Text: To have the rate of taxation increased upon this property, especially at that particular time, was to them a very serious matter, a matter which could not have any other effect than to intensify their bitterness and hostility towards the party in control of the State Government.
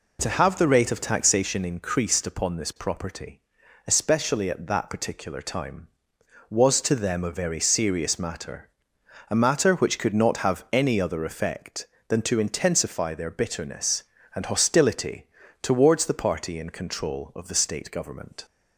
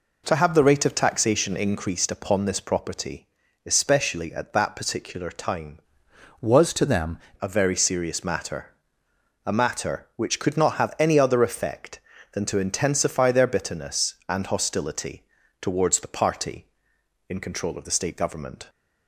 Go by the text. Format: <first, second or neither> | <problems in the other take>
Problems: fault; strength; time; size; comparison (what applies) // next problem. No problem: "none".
first | changes voice from "was" to "them"; from 6.4 to 7.1 s; 0.7 s long // pauses between "hostility" and "towards"; at 15.2 s; 0.38 s long; slight in the first